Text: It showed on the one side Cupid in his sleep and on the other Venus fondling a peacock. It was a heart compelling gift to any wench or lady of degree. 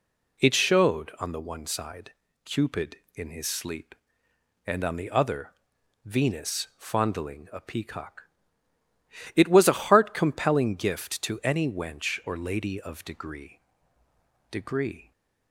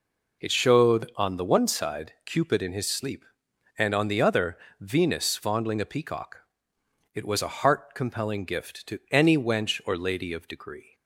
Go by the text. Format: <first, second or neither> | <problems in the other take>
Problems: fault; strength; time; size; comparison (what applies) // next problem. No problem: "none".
second | pauses between "side" and "Cupid"; slight; at 2.1 s; 0.32 s long // pauses between "other" and "Venus"; noticeable; at 5.5 s; 0.54 s long; slight in the second // says "degree" twice; at 14.5 s